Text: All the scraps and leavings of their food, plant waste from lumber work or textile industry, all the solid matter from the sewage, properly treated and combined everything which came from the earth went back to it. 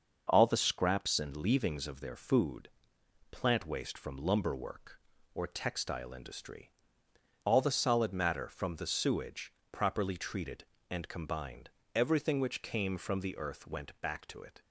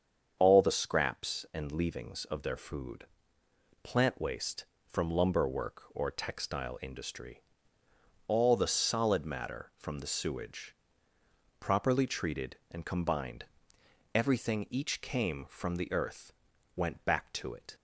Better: first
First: starts louder than the rest; noticeable; until 1.3 s; 6 dB // pauses between "combined" and "everything"; slight; at 11.7 s; 0.24 s long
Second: starts louder than the rest; strong; until 1.3 s; 7 dB // pauses between "combined" and "everything"; noticeable; at 13.4 s; 0.70 s long // says "each" for "which"; at 14.7 s // pauses between "earth" and "went"; noticeable; at 16.3 s; 0.46 s long

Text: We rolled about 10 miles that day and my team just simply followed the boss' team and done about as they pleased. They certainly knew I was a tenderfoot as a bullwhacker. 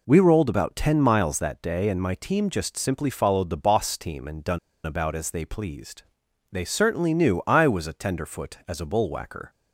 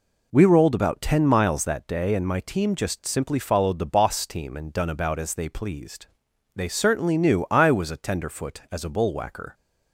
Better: second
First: pauses between "done" and "about"; slight; at 4.5 s; 0.27 s long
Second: none

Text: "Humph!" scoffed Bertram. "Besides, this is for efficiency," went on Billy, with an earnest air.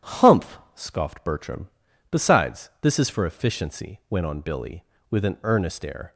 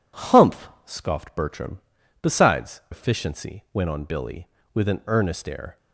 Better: first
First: none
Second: skips "this is for"; at 2.8 s

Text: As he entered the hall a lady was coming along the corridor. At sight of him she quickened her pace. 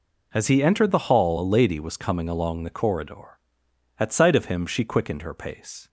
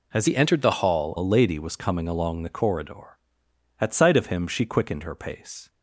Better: first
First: none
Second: changes voice from "he" to "hall"; from 0.2 to 1.1 s; 0.9 s long

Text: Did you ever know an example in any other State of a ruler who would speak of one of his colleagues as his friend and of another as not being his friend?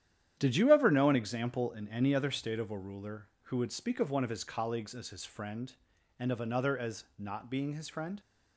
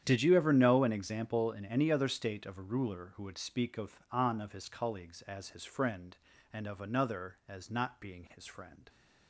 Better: first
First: starts louder than the rest; strong; until 1.4 s; 10.5 dB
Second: starts louder than the rest; strong; until 1.0 s; 9.5 dB // says "on" for "one"; at 4.1 s

